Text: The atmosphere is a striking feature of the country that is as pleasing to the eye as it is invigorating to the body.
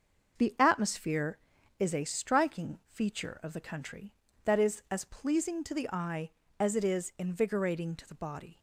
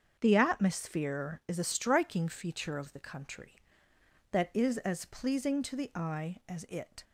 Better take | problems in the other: first | starts louder than the rest; until 1.2 s; 7 dB; also in the first // stops before "is invigorating to the body"; at 7.0 s

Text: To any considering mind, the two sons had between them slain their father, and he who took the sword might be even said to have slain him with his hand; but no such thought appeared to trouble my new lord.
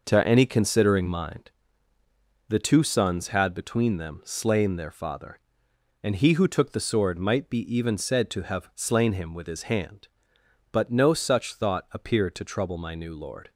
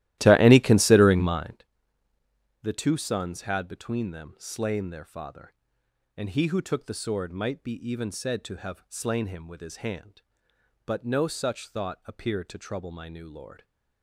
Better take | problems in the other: first | starts louder than the rest; strong; until 1.6 s; 15.5 dB

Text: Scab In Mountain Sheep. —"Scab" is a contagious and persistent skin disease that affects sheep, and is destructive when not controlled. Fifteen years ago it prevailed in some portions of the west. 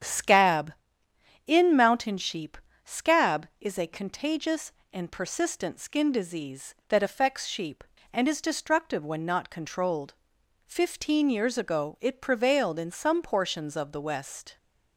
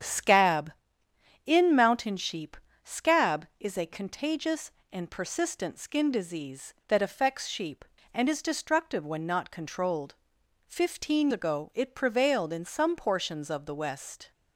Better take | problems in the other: first | starts louder than the rest; strong; until 1.7 s; 8 dB; strong in the first // skips "years"; at 11.3 s

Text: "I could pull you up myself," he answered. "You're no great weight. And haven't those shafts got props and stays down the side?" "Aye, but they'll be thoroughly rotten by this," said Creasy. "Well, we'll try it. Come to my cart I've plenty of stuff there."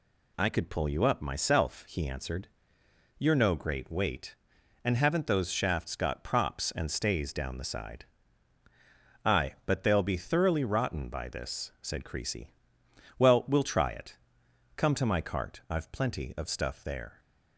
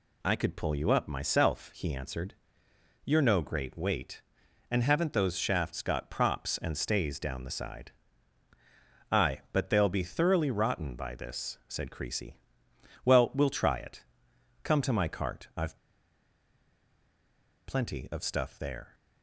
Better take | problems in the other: first | pauses between "I've" and "plenty"; strong; at 15.7 s; 1.8 s long

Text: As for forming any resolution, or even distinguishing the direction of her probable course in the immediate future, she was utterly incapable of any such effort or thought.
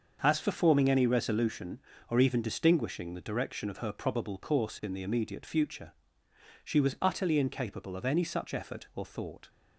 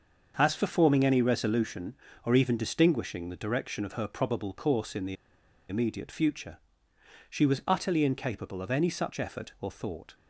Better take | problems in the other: first | starts louder than the rest; until 1.3 s; 6.5 dB; also in the first // pauses between "the" and "immediate"; noticeable; at 5.1 s; 0.54 s long

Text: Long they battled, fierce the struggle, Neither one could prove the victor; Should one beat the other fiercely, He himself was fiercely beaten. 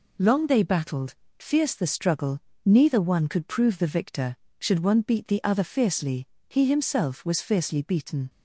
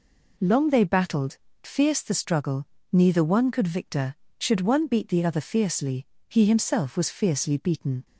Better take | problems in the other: first | skips "prove the"; at 3.6 s

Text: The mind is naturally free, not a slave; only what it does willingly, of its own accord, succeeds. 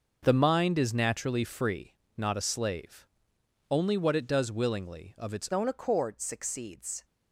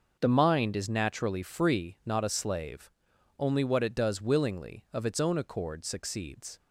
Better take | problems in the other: second | starts louder than the rest; noticeable; until 1.2 s; 6 dB // changes voice at "own"; from 5.5 s on; 1.5 s long

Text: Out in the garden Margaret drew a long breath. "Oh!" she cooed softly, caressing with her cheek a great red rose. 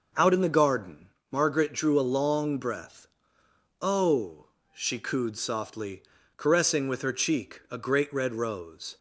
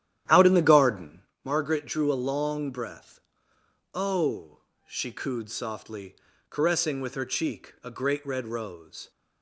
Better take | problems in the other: first | starts louder than the rest; strong; until 1.4 s; 11.5 dB // pauses between "garden" and "Margaret"; slight; at 1.2 s; 0.24 s long; slight in the first

